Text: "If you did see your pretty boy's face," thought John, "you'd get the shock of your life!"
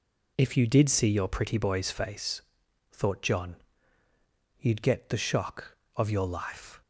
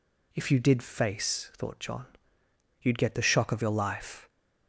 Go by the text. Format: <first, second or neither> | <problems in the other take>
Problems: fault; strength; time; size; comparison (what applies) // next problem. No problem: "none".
first | skips "see your pretty boy's"; at 0.8 s